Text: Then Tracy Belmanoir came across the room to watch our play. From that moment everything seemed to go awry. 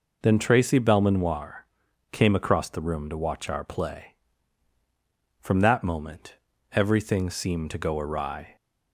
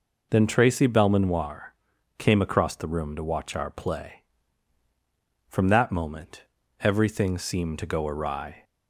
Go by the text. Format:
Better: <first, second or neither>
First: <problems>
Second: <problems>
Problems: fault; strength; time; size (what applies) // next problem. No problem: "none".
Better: neither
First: pauses between "Belmanoir" and "came"; noticeable; at 1.6 s; 0.46 s long // pauses between "moment" and "everything"; slight; at 6.3 s; 0.36 s long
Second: pauses between "Belmanoir" and "came"; at 1.7 s; 0.44 s long // pauses between "moment" and "everything"; slight; at 6.4 s; 0.36 s long